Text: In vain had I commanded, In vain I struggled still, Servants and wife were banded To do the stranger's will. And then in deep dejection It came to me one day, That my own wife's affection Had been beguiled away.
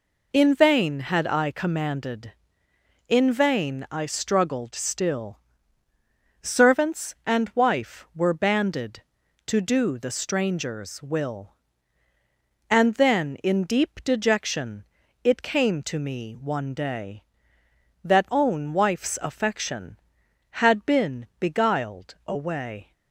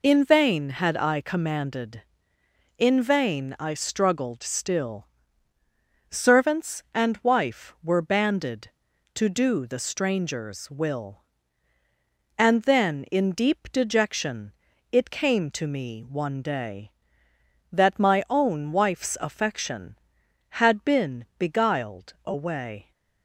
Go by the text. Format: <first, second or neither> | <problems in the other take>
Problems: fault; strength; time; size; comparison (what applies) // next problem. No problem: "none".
second | pauses between "dejection" and "It"; at 14.8 s; 0.40 s long; also in the second // skips "my"; at 18.3 s